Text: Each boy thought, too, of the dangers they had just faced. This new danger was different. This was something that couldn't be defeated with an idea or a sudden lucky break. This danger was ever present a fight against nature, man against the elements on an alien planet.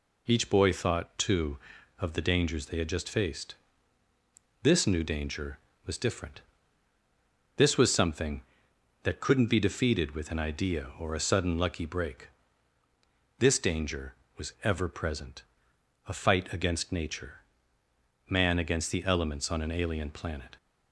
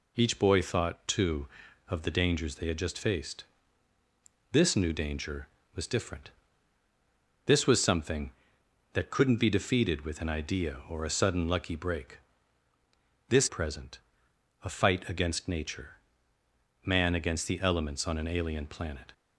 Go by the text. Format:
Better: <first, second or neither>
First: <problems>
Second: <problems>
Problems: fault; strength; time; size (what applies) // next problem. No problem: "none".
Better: first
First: pauses between "present" and "a"; noticeable; at 15.4 s; 0.64 s long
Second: skips "danger was ever"; at 13.4 s // pauses between "present" and "a"; noticeable; at 13.9 s; 0.64 s long